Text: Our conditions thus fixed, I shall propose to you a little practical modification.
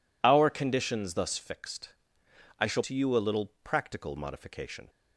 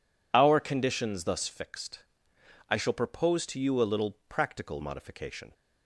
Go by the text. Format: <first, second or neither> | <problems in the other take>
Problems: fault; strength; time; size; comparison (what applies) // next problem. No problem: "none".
second | skips "propose"; at 2.8 s